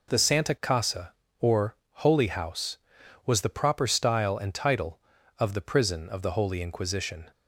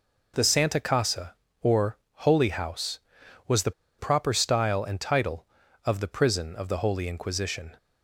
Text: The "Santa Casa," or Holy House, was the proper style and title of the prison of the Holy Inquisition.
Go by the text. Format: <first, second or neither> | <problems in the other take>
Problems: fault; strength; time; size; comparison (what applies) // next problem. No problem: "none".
first | pauses between "or" and "Holy"; slight; at 1.9 s; 0.30 s long; slight in the first // pauses between "the" and "proper"; slight; at 3.7 s; 0.27 s long